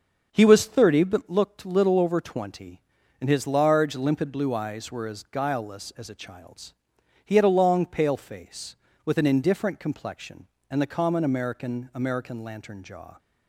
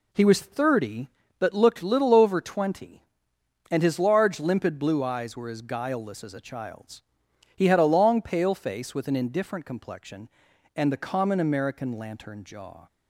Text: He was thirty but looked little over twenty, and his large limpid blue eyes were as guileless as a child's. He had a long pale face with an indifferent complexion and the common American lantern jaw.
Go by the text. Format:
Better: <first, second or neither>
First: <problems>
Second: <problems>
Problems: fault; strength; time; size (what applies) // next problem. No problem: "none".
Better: second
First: starts louder than the rest; noticeable; until 1.3 s; 6 dB // says "American" twice; at 11.9 s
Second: none